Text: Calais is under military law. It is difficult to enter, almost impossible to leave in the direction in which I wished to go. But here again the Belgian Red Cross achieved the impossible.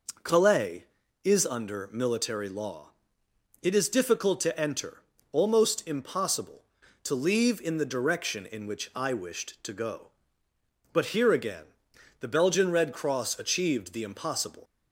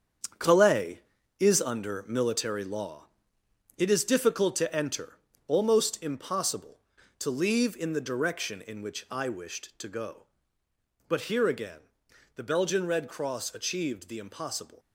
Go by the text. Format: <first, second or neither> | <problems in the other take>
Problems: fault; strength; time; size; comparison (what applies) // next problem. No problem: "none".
first | gets quieter; strong; throughout; 8.5 dB // pauses between "again" and "the"; noticeable; at 11.7 s; 0.56 s long; noticeable in the first